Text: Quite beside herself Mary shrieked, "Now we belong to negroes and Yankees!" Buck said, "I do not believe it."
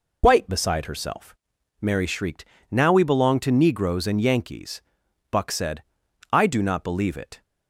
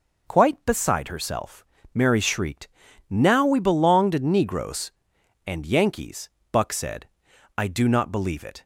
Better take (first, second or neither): second